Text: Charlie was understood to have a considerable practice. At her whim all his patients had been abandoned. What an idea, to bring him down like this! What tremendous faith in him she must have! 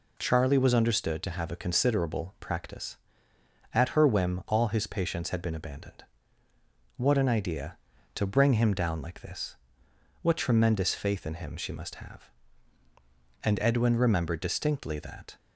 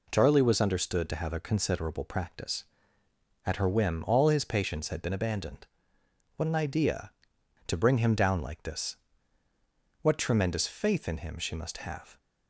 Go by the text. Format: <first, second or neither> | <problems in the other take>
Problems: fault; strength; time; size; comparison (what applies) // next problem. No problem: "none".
second | goes on to say "And Edwin remembered distinctly that"; strong; from 13.4 s on; 1.9 s long